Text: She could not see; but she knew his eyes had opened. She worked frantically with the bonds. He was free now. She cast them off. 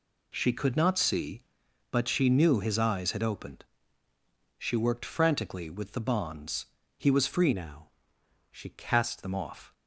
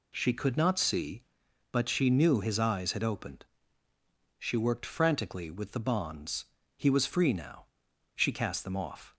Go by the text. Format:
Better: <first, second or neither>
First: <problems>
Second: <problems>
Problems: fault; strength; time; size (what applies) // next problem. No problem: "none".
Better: second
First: changes voice from "now" to "cast"; from 7.5 to 9.2 s; 1.7 s long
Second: none